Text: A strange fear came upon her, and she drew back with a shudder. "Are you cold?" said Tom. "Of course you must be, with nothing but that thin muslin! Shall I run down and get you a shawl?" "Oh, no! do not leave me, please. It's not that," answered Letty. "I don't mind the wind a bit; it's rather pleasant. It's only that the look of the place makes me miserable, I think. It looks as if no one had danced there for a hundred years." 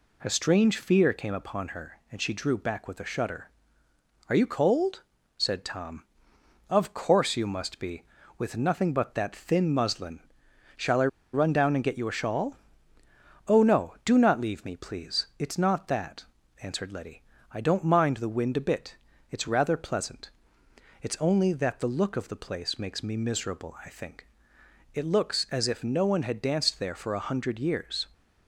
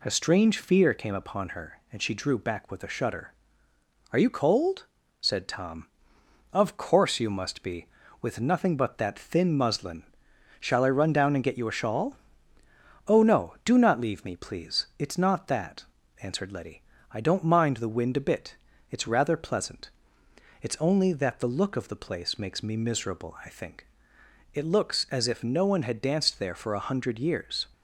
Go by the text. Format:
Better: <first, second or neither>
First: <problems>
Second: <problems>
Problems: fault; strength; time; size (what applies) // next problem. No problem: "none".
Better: second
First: pauses between "I" and "run"; slight; at 11.0 s; 0.26 s long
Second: none